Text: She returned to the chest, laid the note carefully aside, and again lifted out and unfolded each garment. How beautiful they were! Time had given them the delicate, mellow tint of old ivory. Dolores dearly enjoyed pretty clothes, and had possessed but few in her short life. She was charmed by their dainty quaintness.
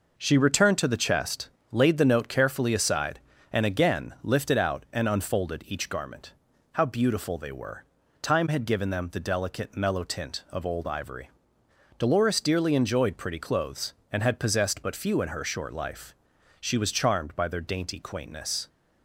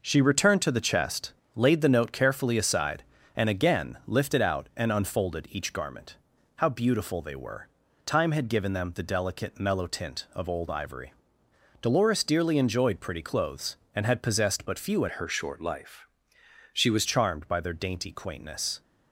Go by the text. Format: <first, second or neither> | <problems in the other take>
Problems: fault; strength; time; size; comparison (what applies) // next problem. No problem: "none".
first | changes voice from "her" to "was"; from 15.1 to 17.0 s; 1.9 s long